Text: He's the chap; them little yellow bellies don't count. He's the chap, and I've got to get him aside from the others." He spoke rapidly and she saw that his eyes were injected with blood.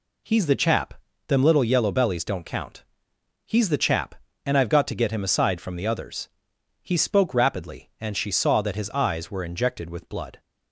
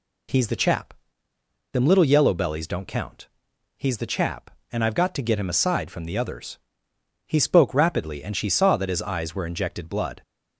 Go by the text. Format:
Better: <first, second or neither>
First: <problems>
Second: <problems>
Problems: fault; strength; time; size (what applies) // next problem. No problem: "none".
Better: first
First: none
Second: skips "with"; at 9.8 s